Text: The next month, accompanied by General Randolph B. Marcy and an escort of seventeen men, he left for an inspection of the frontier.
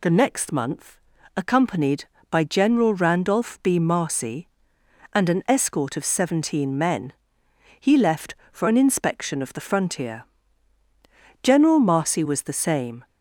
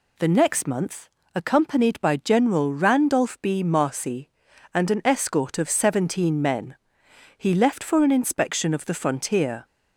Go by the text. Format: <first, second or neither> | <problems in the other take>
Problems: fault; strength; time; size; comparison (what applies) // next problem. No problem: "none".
second | goes on to say "General Marcy was the same"; from 11.4 s on; 1.6 s long